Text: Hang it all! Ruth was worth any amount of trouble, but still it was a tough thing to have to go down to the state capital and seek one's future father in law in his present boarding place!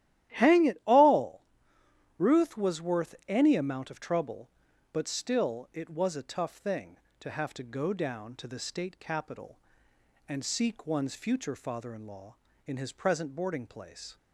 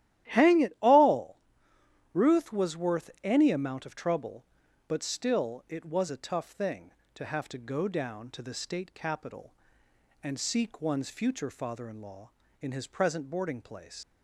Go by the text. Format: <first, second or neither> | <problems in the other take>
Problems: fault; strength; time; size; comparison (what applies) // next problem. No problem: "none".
first | starts louder than the rest; strong; until 1.3 s; 13 dB; strong in the first // leaves "place" unfinished; at 14.0 s; 80 ms